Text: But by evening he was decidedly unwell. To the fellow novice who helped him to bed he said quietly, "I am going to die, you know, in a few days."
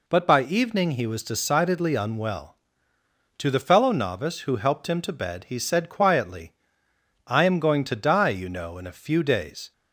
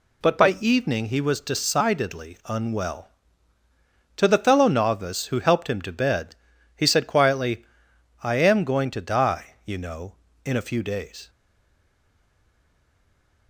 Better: first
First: none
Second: pauses between "bed" and "he"; at 6.3 s; 0.40 s long // stays silent after the last word; from 11.2 s on; 2.2 s long

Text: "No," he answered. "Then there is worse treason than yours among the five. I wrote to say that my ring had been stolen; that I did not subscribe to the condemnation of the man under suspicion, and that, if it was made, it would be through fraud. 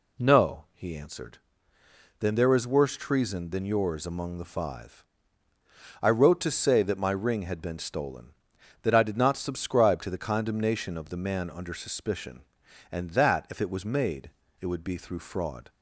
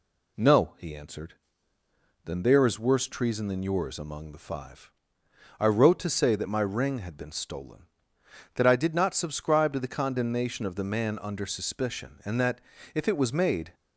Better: first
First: none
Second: stops before "it would be through fraud"; at 13.7 s

